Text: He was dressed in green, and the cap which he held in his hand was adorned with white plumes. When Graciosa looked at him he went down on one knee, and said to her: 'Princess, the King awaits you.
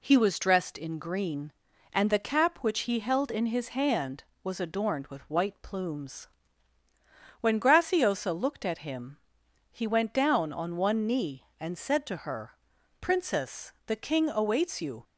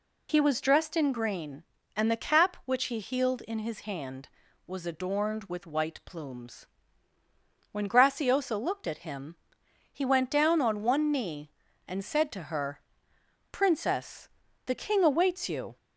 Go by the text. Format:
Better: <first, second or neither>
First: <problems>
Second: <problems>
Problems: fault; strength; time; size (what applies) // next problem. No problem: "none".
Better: first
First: pauses between "him" and "he"; noticeable; at 9.1 s; 0.54 s long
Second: says "healed" for "held"; at 2.9 s // pauses between "him" and "he"; noticeable; at 9.3 s; 0.54 s long